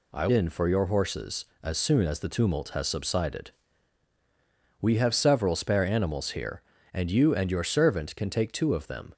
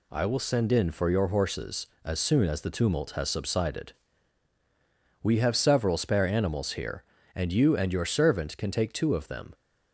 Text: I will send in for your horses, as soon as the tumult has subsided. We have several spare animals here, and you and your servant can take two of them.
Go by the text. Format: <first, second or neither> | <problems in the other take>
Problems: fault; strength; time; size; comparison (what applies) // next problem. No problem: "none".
second | skips "will send"; at 0.2 s